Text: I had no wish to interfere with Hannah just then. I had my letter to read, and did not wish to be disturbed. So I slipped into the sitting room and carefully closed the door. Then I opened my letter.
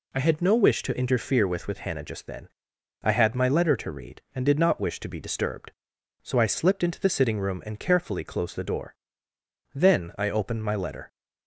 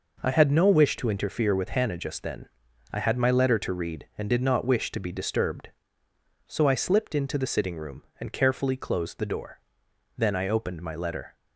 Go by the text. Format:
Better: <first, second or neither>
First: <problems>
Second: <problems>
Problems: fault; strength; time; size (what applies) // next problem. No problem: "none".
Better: second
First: says "with" twice; at 1.6 s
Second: none